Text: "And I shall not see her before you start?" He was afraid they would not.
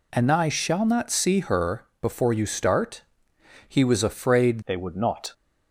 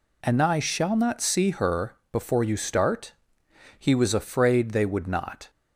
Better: second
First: pauses between "her" and "before"; slight; at 1.8 s; 0.16 s long // changes voice at "they"; from 4.6 s on; 0.7 s long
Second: pauses between "her" and "before"; slight; at 1.9 s; 0.16 s long

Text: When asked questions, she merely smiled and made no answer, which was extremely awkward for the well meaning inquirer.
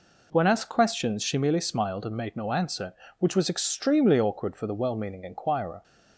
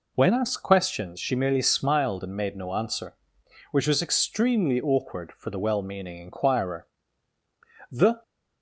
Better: first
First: none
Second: goes on to say "The"; slight; from 7.9 s on; 0.32 s long

